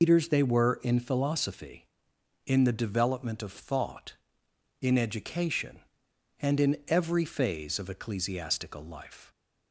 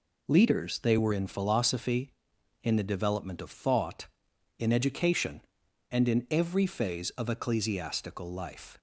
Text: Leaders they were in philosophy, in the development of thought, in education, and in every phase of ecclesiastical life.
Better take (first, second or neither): second